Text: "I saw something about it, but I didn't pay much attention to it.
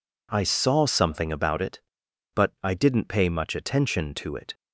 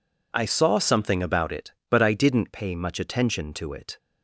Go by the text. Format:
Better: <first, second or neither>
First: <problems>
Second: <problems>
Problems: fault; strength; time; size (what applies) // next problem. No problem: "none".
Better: neither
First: none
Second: none